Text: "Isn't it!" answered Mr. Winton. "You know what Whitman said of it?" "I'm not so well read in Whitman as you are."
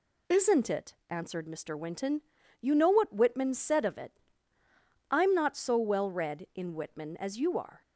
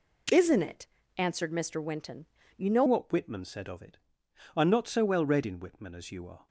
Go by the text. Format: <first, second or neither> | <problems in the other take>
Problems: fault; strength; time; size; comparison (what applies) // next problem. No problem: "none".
first | changes voice at "what"; from 2.8 s on; 3.6 s long